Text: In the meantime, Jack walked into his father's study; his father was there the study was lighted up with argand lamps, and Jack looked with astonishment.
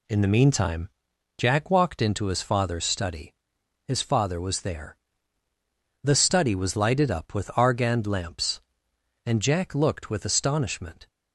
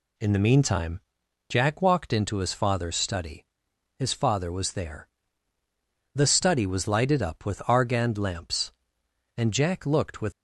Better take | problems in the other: first | pauses between "there" and "the"; at 5.0 s; 1.0 s long; also in the first // stops before "astonishment"; at 10.3 s

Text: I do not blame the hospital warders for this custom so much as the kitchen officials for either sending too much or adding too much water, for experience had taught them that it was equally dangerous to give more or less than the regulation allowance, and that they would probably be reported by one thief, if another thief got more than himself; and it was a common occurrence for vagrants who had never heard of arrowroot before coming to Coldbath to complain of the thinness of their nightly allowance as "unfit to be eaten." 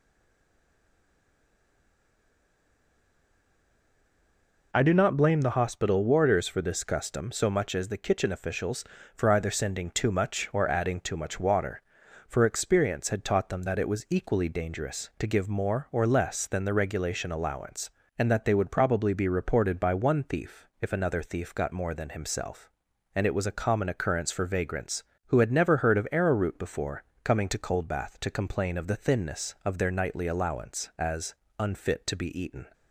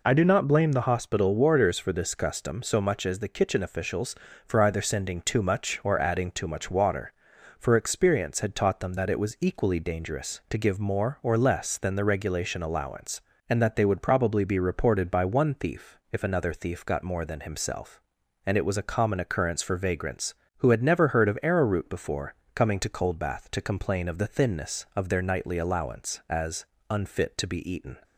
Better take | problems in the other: second | stays silent before the first word; strong; until 4.7 s; 4.7 s long // pauses between "before" and "coming"; slight; at 27.0 s; 0.22 s long; slight in the second // pauses between "as" and "unfit"; slight; at 31.3 s; 0.26 s long; slight in the second

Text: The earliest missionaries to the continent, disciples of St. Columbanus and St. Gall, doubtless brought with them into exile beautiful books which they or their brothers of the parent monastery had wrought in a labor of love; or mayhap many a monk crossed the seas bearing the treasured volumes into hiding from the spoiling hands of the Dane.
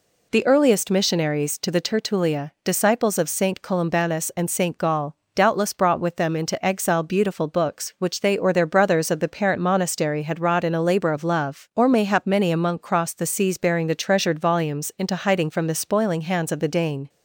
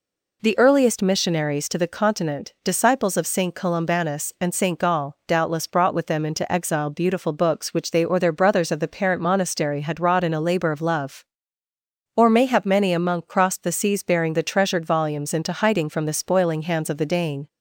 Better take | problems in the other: second | says "tertulia" for "continent"; at 1.8 s

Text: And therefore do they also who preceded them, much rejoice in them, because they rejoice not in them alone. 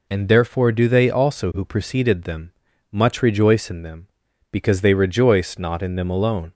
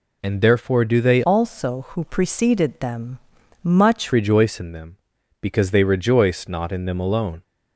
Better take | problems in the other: first | changes voice from "also" to "much"; from 1.2 to 4.1 s; 2.9 s long

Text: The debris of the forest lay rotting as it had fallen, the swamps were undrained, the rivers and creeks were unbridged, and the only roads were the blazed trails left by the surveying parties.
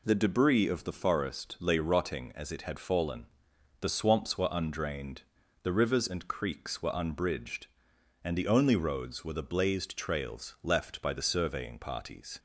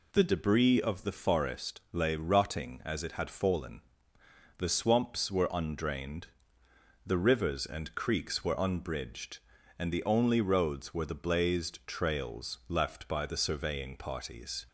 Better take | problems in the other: neither | none

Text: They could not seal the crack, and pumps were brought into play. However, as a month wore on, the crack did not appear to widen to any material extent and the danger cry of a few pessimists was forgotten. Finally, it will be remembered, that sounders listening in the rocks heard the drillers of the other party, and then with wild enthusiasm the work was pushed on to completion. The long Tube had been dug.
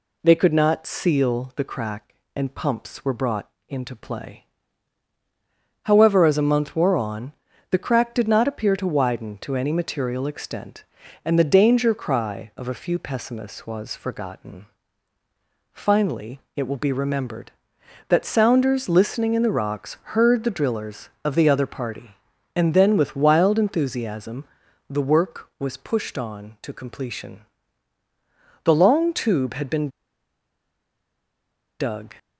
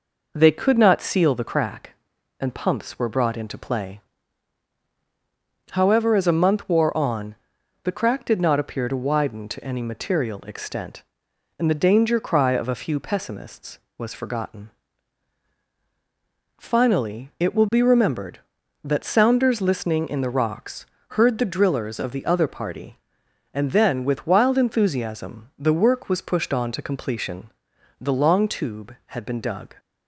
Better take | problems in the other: second | pauses between "brought" and "into"; slight; at 3.4 s; 0.20 s long // pauses between "rocks" and "heard"; slight; at 19.9 s; 0.16 s long; slight in the second // pauses between "enthusiasm" and "the"; noticeable; at 24.4 s; 0.46 s long // pauses between "been" and "dug"; strong; at 29.8 s; 1.9 s long

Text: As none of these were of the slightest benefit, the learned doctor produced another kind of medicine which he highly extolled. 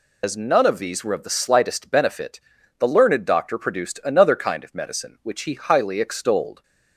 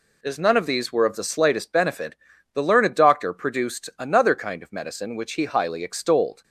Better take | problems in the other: second | loses the start of "As"; at 0.2 s; 90 ms

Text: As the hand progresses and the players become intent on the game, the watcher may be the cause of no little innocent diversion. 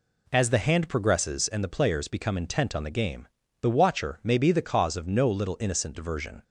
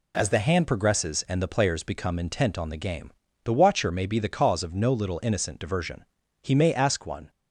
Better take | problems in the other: first | goes on to say "He may ask one"; noticeable; from 6.4 s on; 0.88 s long

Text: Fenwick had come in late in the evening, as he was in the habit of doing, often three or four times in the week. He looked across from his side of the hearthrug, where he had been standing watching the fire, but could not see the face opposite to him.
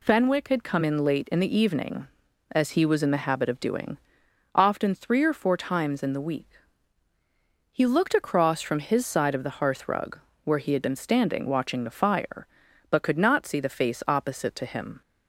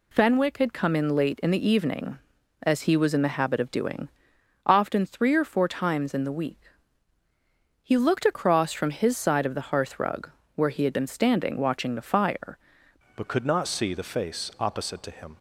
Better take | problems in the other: first | changes voice at "but"; from 13.1 s on; 2.2 s long

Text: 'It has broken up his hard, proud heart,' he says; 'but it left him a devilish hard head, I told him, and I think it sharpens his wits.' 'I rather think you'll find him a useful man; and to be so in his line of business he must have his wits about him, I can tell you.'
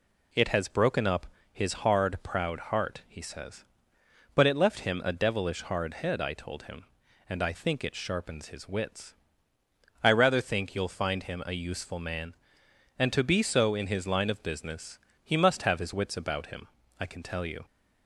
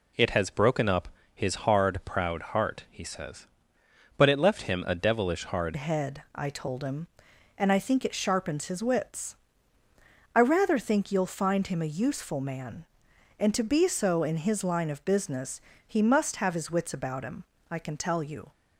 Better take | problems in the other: first | pauses between "up" and "his"; slight; at 1.0 s; 0.26 s long; slight in the first // changes voice at "head"; from 5.7 s on; 12.8 s long // pauses between "business" and "he"; slight; at 15.6 s; 0.24 s long; slight in the first

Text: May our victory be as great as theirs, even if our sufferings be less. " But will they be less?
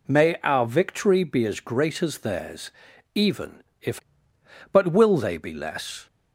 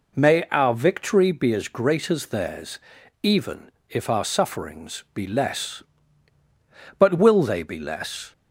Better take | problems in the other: second | pauses between "even" and "if"; slight; at 3.6 s; 0.18 s long; slight in the second // skips "our sufferings be less"; at 4.0 s

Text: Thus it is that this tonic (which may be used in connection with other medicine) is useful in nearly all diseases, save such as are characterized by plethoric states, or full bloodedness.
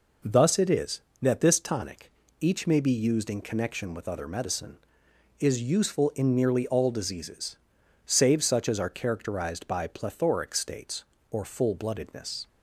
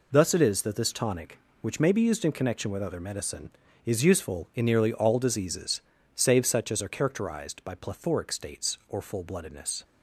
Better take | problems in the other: second | says "each" for "which"; at 2.3 s

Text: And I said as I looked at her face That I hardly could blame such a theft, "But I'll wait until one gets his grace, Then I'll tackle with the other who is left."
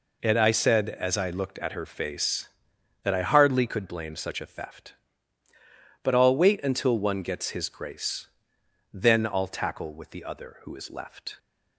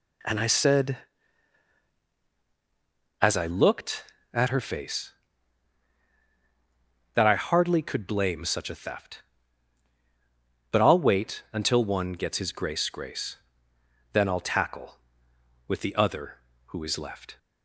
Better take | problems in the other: first | says "grace" twice; at 12.8 s

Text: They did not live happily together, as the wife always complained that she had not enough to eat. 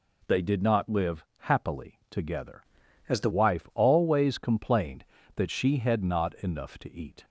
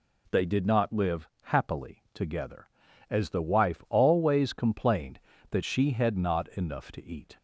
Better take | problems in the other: second | changes voice from "as" to "the"; from 3.0 to 3.2 s; 0.2 s long

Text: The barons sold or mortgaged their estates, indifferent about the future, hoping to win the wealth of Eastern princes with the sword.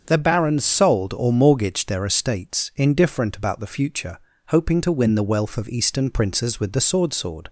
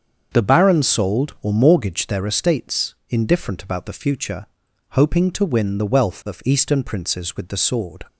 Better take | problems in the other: second | starts louder than the rest; until 1.0 s; 7 dB; also in the second // says "sword" twice; at 7.1 s

